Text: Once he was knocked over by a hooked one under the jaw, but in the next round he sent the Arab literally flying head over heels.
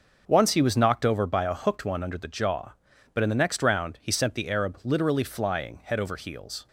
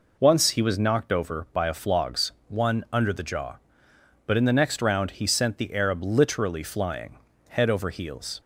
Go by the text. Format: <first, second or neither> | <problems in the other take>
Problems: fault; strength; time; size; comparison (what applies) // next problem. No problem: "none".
first | says "flogs" for "hooked"; at 1.7 s // pauses between "flying" and "head"; slight; at 7.1 s; 0.30 s long